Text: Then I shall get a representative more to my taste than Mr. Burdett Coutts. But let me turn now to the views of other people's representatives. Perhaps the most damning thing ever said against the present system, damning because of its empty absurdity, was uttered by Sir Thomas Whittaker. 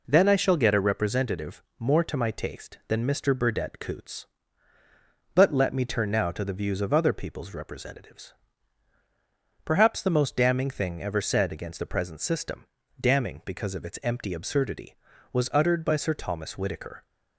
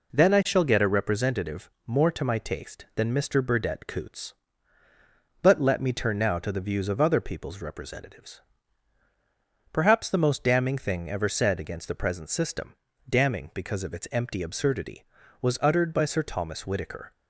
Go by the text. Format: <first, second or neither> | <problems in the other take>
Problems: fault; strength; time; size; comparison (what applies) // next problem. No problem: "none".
neither | pauses between "representative" and "more"; slight; the same in both